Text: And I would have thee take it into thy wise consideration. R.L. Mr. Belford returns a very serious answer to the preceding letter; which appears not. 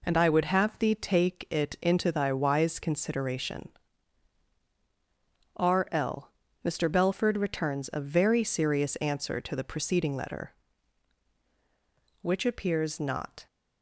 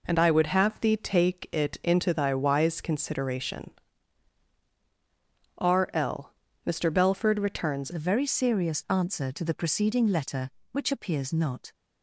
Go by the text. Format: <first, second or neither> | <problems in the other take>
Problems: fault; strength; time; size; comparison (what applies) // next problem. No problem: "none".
first | changes voice at "a"; from 7.9 s on; 3.8 s long